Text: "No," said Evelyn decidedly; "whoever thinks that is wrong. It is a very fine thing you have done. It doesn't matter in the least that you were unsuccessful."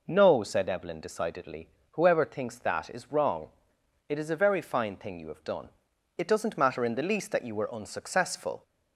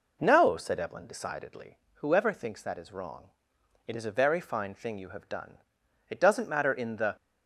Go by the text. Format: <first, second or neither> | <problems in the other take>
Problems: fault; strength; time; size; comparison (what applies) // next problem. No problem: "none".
first | stops before "least that you were unsuccessful"; at 7.1 s